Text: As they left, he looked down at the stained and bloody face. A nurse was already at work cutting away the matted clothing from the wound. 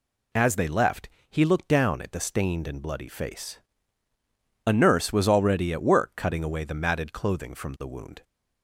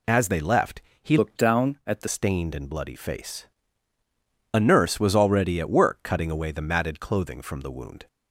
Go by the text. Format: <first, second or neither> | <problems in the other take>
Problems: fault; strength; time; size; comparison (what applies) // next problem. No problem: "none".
first | changes voice from "looked" to "the"; from 1.1 to 2.0 s; 0.9 s long